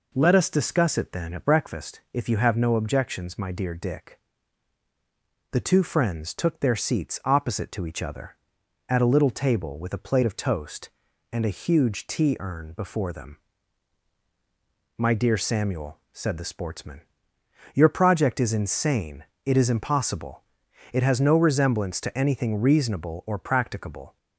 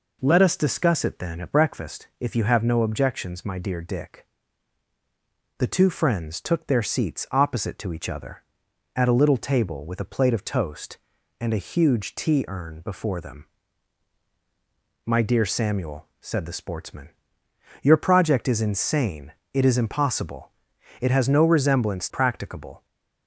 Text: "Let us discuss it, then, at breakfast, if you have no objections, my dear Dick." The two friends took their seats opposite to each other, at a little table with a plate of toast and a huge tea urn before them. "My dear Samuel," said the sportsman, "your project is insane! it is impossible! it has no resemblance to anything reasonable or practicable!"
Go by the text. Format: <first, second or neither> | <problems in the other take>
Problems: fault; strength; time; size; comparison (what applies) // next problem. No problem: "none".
first | skips "to anything reasonable or"; at 22.0 s